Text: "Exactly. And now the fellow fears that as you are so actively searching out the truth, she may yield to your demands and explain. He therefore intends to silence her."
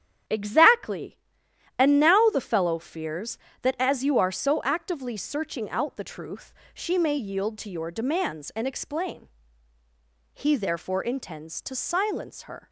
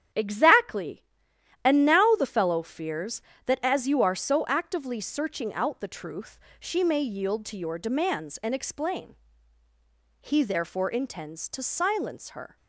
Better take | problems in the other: neither | starts louder than the rest; strong; the same in both

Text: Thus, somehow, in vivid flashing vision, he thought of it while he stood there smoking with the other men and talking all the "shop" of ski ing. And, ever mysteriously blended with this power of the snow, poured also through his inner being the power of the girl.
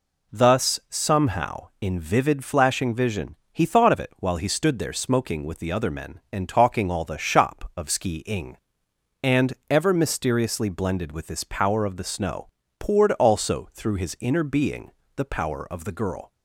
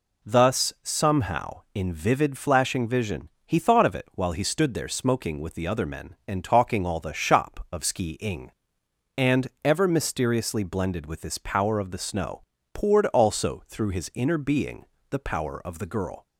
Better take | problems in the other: neither | pauses between "being" and "the"; slight; the same in both

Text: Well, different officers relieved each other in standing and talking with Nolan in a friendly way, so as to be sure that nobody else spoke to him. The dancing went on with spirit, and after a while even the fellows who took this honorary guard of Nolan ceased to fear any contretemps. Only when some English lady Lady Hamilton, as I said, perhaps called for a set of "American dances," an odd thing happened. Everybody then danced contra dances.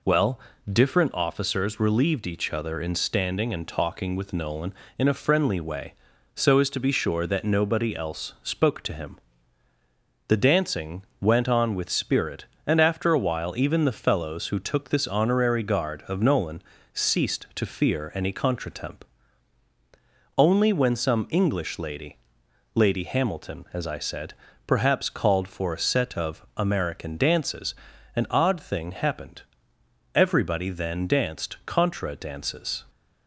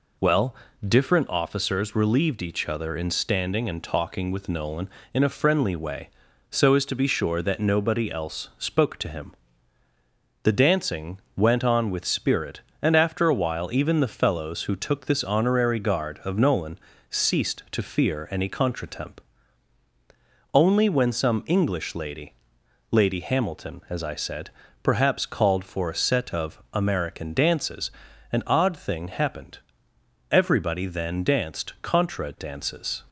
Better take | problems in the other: neither | pauses between "dancing" and "went"; slight; the same in both // pauses between "Nolan" and "ceased"; slight; the same in both // pauses between "lady" and "Lady"; noticeable; the same in both

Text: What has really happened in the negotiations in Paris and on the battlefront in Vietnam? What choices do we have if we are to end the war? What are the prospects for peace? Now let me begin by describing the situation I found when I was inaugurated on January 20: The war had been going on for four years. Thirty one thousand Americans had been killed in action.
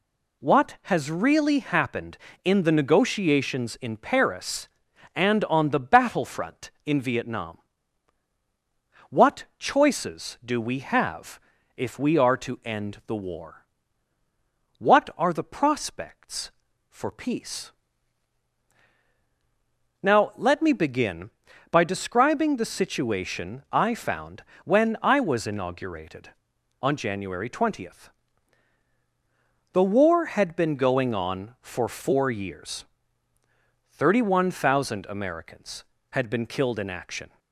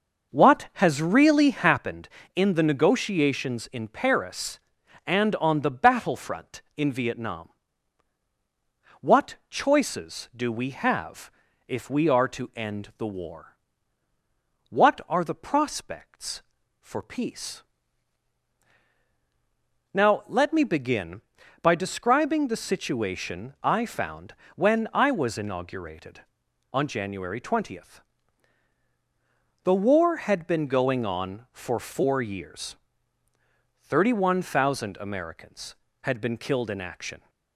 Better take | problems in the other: first | starts louder than the rest; noticeable; until 1.9 s; 5.5 dB // pauses between "have" and "if"; slight; at 11.3 s; 0.36 s long; slight in the first // pauses between "found" and "when"; slight; at 24.3 s; 0.22 s long; slight in the first

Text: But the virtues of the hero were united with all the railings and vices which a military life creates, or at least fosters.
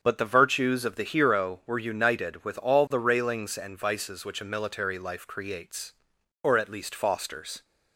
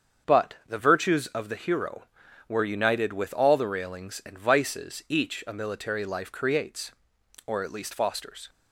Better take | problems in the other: first | starts louder than the rest; strong; until 1.4 s; 7 dB; strong in the first // says "each" for "which"; at 5.0 s

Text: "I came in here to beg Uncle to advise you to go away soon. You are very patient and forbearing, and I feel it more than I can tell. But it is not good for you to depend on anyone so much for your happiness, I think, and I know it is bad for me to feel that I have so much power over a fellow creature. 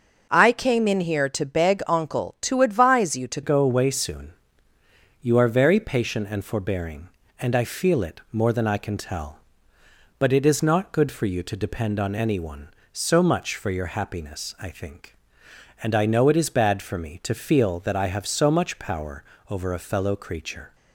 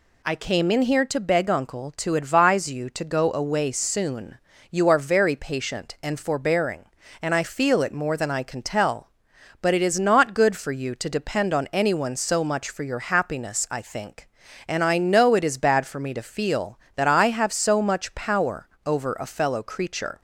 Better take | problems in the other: second | changes voice at "go"; from 3.4 s on; 17.3 s long // pauses between "power" and "over"; slight; at 19.2 s; 0.26 s long; slight in the second

